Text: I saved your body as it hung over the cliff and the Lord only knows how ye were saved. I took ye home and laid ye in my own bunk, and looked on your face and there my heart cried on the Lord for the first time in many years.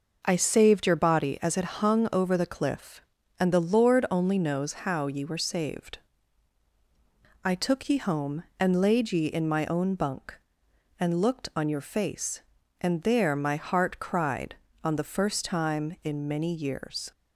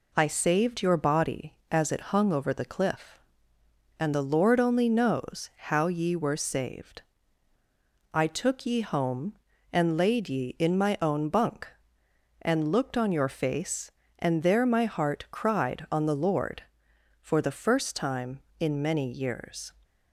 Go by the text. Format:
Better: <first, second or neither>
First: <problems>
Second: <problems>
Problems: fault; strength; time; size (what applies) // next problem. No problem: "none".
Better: second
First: skips "Lord for the"; at 15.0 s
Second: none